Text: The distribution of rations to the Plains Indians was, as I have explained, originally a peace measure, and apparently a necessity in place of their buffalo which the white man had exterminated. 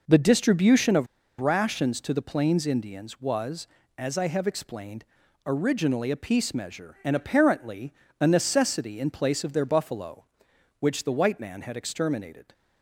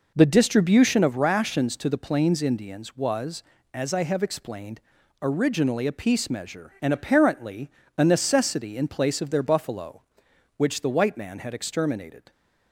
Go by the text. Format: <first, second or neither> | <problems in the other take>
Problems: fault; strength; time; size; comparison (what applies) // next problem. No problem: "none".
second | pauses between "of" and "rations"; slight; at 1.0 s; 0.34 s long // pauses between "apparently" and "a"; slight; at 7.9 s; 0.30 s long; slight in the second